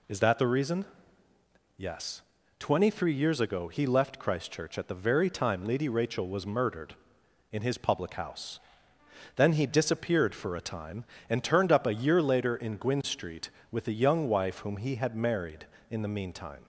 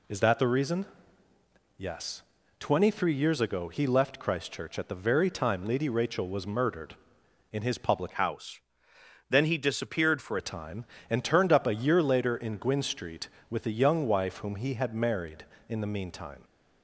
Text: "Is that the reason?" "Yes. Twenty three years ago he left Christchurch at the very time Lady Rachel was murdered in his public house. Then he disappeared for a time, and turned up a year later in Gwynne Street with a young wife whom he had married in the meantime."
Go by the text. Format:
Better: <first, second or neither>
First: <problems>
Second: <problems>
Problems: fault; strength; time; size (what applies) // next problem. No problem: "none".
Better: first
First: none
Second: changes voice from "house" to "for"; from 8.1 to 10.3 s; 2.2 s long